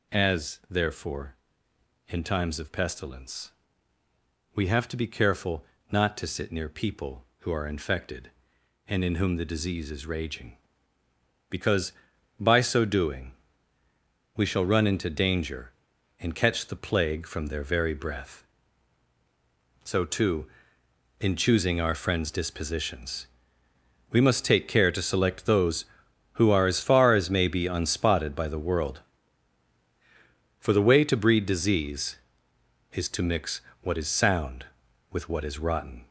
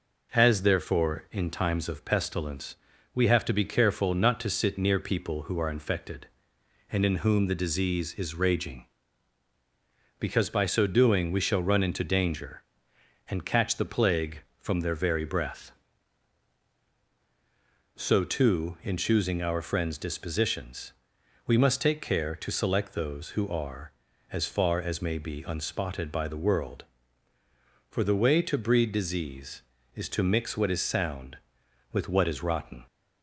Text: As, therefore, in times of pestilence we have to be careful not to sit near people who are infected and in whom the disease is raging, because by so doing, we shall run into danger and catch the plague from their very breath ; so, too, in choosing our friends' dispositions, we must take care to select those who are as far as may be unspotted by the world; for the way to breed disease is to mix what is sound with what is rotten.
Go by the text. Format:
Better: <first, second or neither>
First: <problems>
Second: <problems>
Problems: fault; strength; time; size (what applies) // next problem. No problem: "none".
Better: second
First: gets louder; noticeable; throughout; 5.5 dB // pauses between "pestilence" and "we"; at 3.5 s; 1.0 s long // pauses between "careful" and "not"; slight; at 5.6 s; 0.28 s long // pauses between "mix" and "what"; slight; at 33.6 s; 0.20 s long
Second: pauses between "pestilence" and "we"; slight; at 2.7 s; 0.36 s long